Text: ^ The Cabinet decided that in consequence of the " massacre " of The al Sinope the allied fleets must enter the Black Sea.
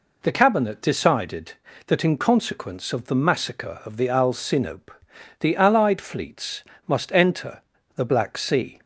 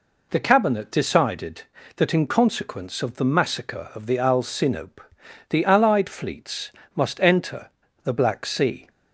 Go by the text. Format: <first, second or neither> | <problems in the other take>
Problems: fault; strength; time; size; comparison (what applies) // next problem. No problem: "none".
neither | pauses between "Sinope" and "the"; noticeable; the same in both // pauses between "fleets" and "must"; slight; the same in both // pauses between "enter" and "the"; slight; the same in both